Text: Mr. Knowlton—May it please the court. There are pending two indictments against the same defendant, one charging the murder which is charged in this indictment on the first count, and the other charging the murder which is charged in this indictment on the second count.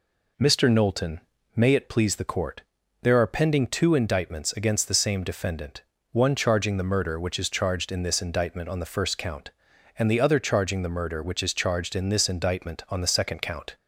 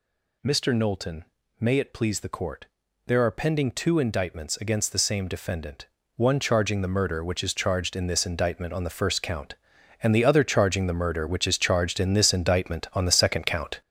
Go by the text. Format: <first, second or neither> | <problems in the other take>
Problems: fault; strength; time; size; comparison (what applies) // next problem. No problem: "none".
first | gets louder; throughout; 7 dB